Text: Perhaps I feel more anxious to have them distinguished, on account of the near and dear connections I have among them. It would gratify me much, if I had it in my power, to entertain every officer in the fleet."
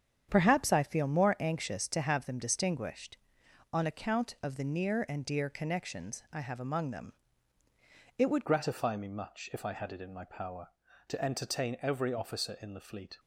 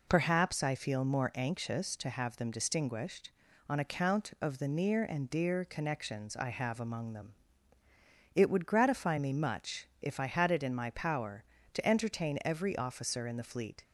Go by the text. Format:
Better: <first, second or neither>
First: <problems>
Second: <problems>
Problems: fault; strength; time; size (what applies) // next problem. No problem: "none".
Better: second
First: starts louder than the rest; strong; until 1.3 s; 8.5 dB // changes voice at "gratify"; from 8.4 s on; 4.7 s long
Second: none